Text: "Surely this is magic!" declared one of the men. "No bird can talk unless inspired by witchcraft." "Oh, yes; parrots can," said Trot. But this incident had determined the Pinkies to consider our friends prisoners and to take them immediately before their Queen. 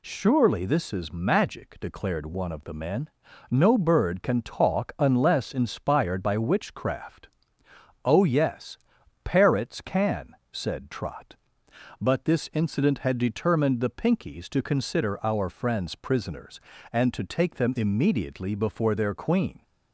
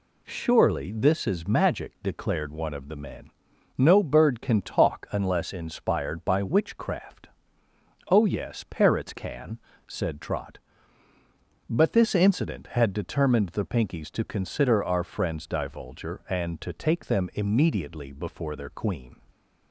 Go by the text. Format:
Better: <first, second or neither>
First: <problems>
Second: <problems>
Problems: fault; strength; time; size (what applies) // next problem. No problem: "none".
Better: first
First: none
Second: says "divulger" for "prisoners"; at 15.4 s